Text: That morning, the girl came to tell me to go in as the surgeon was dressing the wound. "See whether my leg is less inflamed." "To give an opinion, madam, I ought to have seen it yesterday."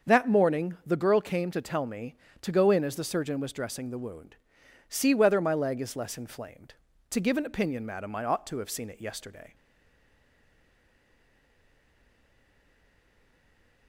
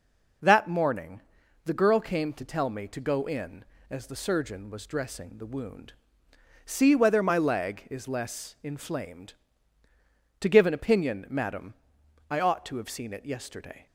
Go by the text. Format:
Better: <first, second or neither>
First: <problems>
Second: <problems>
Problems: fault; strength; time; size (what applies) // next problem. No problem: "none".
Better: second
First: starts louder than the rest; until 1.1 s; 7 dB // stays silent after the last word; strong; from 9.5 s on; 4.3 s long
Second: none